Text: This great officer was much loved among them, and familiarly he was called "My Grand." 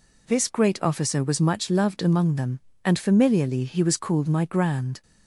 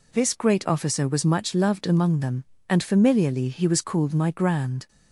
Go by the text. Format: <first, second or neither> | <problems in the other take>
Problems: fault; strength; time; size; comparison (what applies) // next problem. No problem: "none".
neither | none